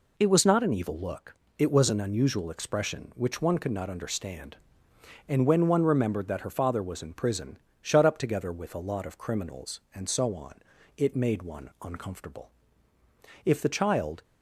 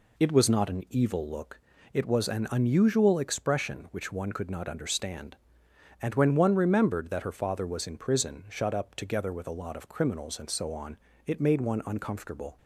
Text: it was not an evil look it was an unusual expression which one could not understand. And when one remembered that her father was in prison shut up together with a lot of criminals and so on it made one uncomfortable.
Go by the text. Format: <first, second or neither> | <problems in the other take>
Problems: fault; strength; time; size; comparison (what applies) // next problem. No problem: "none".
second | pauses between "look" and "it"; slight; at 1.3 s; 0.24 s long; slight in the second // pauses between "prison" and "shut"; slight; at 7.5 s; 0.24 s long // pauses between "on" and "it"; at 10.5 s; 0.42 s long; slight in the second // goes on to say "If the child"; noticeable; from 13.4 s on; 0.78 s long